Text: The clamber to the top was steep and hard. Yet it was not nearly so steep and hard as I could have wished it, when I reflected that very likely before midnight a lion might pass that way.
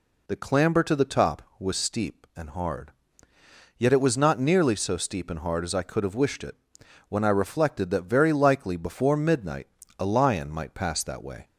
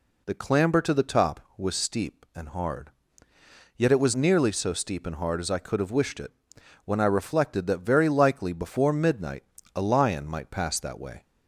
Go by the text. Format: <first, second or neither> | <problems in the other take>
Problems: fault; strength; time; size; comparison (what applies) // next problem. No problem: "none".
first | skips "not"; at 4.1 s // pauses between "midnight" and "a"; slight; at 9.4 s; 0.32 s long; slight in the first